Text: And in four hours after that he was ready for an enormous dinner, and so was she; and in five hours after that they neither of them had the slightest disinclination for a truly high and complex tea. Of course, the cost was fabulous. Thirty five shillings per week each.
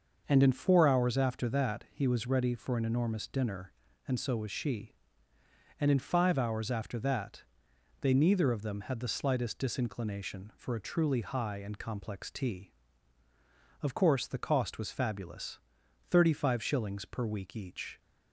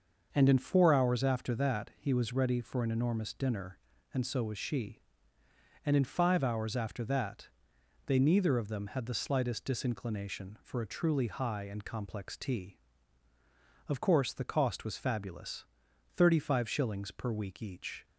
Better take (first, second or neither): neither